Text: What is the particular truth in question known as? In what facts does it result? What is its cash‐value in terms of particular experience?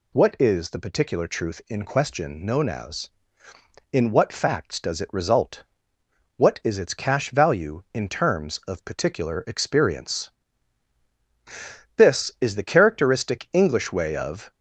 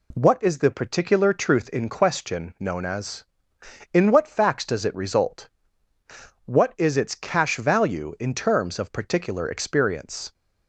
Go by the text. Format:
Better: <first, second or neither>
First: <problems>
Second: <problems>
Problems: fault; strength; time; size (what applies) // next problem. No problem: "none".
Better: second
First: goes on to say "This is the characteristic English way of"; strong; from 11.9 s on; 2.5 s long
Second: none